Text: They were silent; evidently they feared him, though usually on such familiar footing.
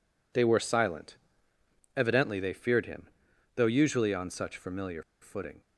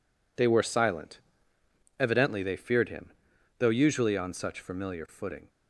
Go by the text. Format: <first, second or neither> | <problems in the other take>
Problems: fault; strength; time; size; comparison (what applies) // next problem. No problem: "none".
second | pauses between "familiar" and "footing"; slight; at 5.0 s; 0.19 s long